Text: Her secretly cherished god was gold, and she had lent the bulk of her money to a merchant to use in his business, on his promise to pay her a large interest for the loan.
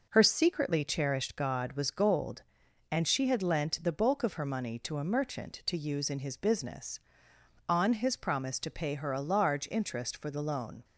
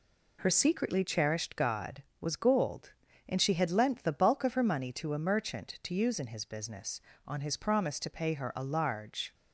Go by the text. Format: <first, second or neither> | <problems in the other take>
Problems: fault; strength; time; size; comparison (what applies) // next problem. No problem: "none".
first | stops before "interest for the loan"; at 9.3 s